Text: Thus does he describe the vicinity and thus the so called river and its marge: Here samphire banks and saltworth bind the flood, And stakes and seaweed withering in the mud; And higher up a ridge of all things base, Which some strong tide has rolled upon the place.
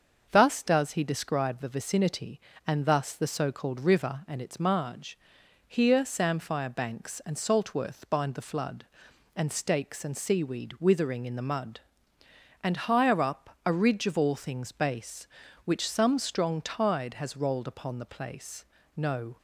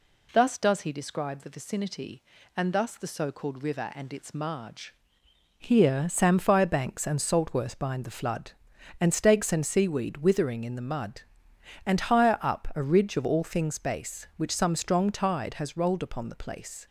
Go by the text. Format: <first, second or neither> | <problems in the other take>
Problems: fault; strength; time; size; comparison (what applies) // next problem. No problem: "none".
second | starts louder than the rest; until 1.3 s; 6.5 dB // goes on to say "No"; slight; from 18.9 s on; 0.40 s long